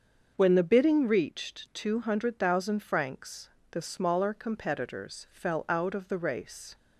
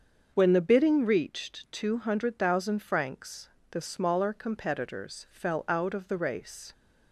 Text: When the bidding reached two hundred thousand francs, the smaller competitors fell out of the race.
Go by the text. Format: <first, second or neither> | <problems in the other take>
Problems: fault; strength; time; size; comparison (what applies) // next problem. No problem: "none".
neither | starts louder than the rest; the same in both